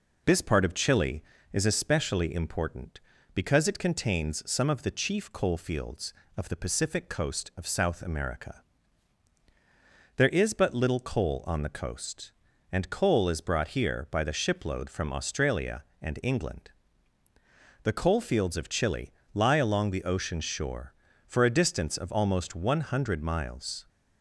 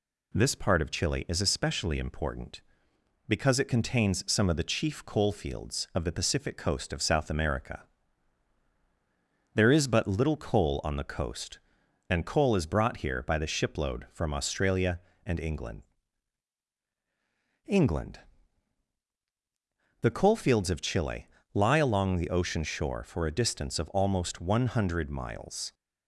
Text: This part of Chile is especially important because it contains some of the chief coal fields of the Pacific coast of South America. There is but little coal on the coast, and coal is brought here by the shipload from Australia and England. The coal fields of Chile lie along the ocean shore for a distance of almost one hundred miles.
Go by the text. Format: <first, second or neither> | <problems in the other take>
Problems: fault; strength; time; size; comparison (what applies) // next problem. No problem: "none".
first | says "England" twice; at 17.6 s // pauses between "Chile" and "lie"; slight; at 21.2 s; 0.26 s long; slight in the first